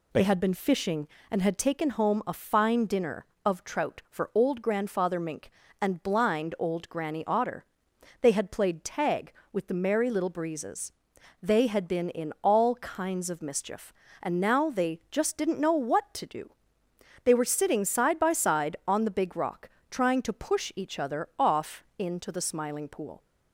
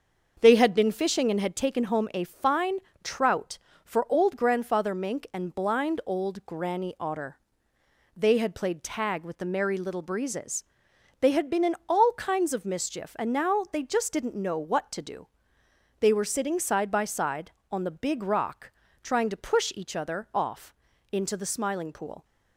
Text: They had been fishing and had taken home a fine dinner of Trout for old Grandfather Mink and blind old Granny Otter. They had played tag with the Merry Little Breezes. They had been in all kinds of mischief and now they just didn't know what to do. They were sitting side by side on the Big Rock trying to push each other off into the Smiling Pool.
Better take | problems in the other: first | starts louder than the rest; until 1.4 s; 6.5 dB // skips "dinner of"; at 2.8 s // pauses between "Rock" and "trying"; slight; at 18.6 s; 0.32 s long; slight in the first // pauses between "off" and "into"; slight; at 20.7 s; 0.36 s long

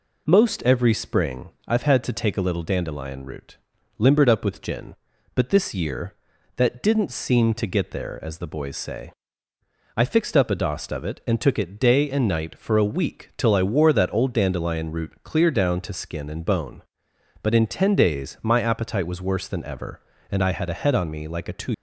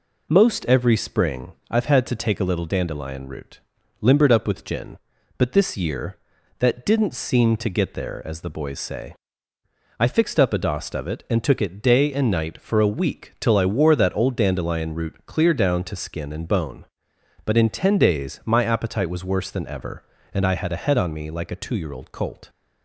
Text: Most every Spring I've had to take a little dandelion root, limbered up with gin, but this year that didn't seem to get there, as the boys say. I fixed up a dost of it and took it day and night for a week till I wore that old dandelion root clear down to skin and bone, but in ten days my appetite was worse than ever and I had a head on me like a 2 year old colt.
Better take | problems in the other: second | pauses between "Spring" and "I've"; slight; at 1.4 s; 0.18 s long; slight in the second // stops before "year old colt"; at 21.7 s

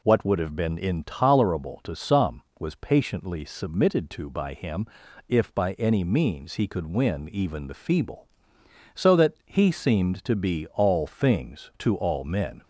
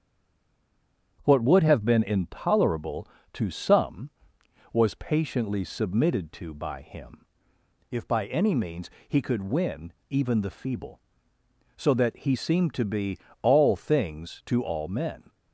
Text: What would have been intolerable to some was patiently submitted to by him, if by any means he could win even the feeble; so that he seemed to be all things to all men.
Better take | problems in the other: first | stays silent before the first word; noticeable; until 1.1 s; 1.1 s long // starts louder than the rest; strong; until 2.2 s; 8 dB // pauses between "means" and "he"; slight; at 8.8 s; 0.18 s long // pauses between "win" and "even"; slight; at 9.9 s; 0.18 s long // pauses between "be" and "all"; slight; at 13.1 s; 0.24 s long

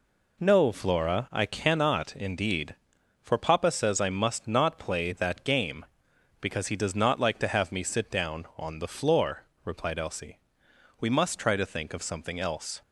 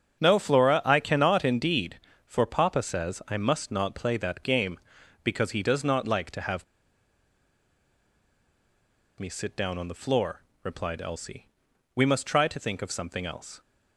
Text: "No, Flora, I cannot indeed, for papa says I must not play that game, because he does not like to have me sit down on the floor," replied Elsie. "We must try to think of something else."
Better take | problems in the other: first | starts louder than the rest; strong; until 1.2 s; 8 dB // pauses between "have" and "me"; strong; at 6.6 s; 2.5 s long

